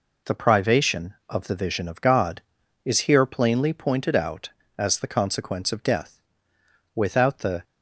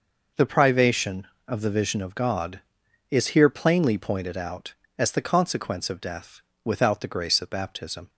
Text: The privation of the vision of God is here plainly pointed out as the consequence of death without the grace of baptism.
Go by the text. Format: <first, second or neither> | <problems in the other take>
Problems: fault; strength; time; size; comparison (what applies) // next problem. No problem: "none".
second | pauses between "death" and "without"; noticeable; at 6.1 s; 0.76 s long; slight in the second // stops before "grace of baptism"; at 7.6 s